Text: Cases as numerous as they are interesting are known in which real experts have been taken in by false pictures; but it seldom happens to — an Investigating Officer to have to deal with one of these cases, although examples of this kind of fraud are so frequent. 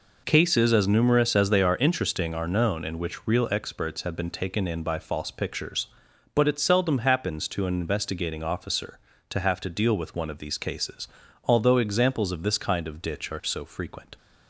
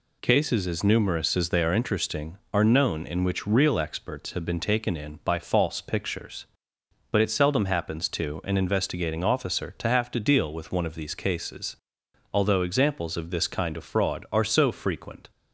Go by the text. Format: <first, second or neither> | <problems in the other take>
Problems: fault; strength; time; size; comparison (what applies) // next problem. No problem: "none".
second | says "ditch" for "fraud"; at 13.0 s